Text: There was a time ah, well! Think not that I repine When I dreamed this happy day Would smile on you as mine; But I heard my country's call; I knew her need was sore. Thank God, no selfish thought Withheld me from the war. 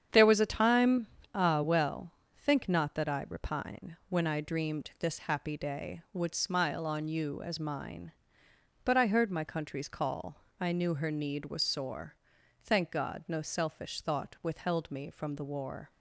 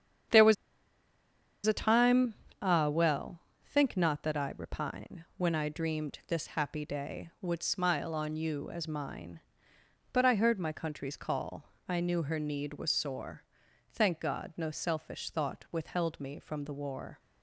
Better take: first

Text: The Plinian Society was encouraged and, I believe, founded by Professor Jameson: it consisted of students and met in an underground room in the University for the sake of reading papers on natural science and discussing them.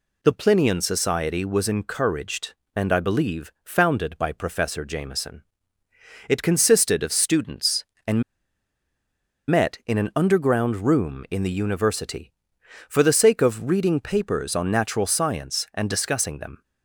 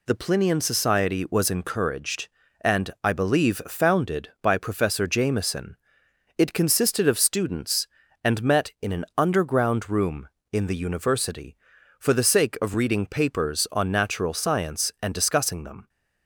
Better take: second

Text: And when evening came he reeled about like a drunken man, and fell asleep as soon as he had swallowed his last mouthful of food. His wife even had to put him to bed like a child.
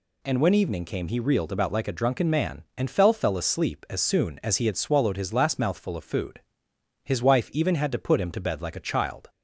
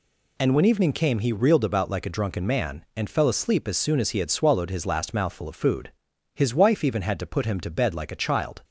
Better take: second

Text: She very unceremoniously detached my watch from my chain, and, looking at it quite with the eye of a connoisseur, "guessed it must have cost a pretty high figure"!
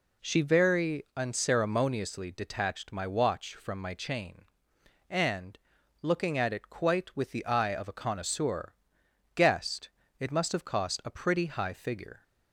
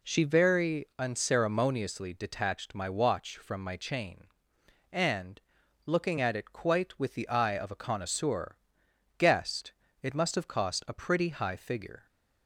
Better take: neither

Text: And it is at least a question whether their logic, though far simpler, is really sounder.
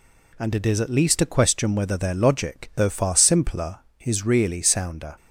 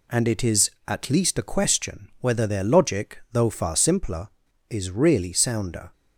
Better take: neither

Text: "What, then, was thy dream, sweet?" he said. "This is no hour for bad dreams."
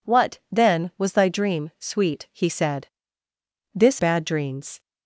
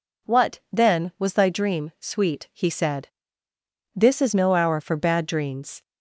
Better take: second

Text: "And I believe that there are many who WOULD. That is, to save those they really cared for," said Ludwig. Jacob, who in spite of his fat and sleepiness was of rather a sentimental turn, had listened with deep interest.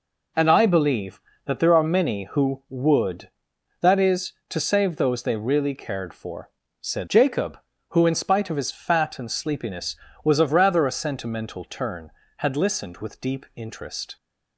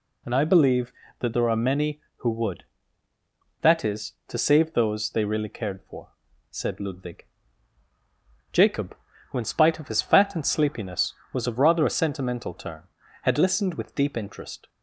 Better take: second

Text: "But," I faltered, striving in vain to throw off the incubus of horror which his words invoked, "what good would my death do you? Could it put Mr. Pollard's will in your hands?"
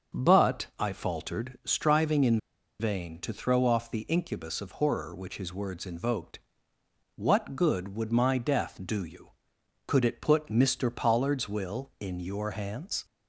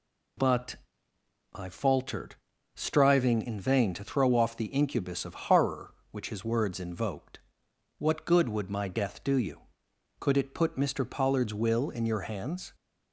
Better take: second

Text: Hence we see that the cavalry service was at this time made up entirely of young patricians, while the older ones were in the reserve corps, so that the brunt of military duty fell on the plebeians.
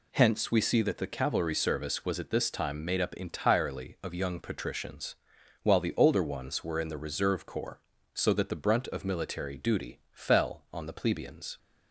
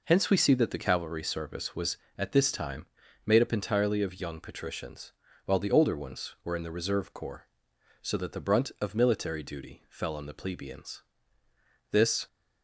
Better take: first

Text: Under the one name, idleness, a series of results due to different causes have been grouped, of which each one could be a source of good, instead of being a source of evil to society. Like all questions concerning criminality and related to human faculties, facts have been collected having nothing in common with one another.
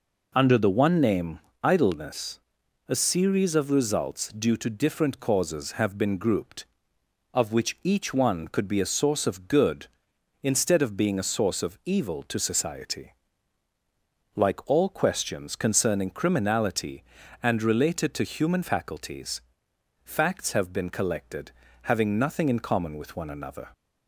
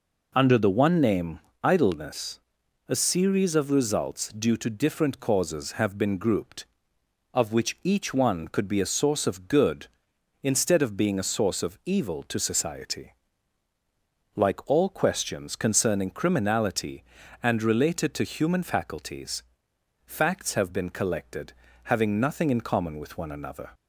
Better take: neither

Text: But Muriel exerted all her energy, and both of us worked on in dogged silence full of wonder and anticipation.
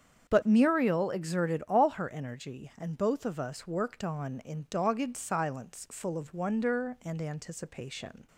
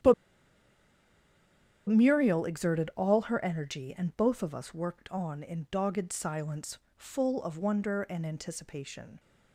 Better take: first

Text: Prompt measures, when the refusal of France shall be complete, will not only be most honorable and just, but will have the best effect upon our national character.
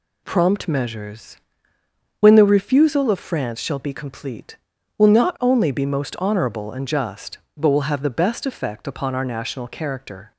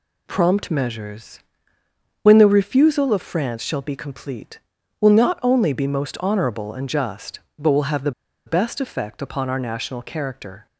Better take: first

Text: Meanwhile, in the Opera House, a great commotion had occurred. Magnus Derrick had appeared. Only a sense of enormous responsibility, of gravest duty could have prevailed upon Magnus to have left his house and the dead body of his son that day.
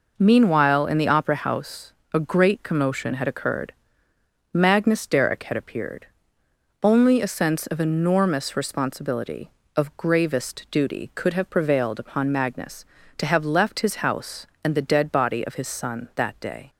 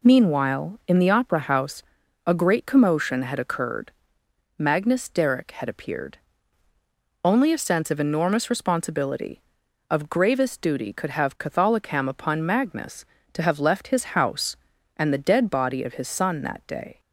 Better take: first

